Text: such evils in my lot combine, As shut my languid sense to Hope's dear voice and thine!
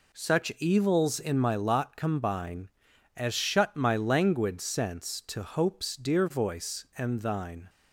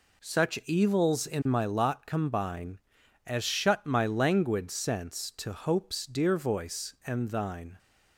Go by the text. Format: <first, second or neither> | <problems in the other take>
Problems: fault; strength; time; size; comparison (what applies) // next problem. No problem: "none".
neither | none